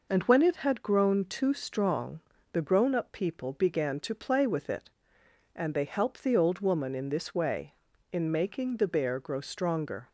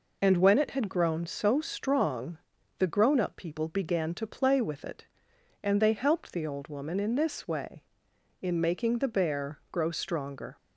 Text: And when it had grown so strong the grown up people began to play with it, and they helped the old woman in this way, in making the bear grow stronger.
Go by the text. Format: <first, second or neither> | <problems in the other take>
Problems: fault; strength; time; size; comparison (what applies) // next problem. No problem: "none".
second | says "too" for "so"; at 1.2 s // pauses between "strong" and "the"; slight; at 2.1 s; 0.34 s long; also in the second